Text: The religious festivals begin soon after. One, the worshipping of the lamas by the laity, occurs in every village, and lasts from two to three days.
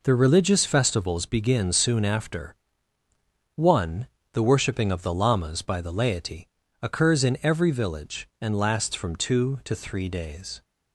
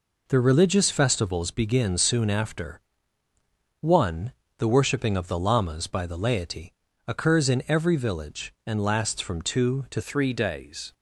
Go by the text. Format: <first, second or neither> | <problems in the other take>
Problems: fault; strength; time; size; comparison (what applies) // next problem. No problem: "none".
first | changes voice at "three"; from 10.0 s on; 0.9 s long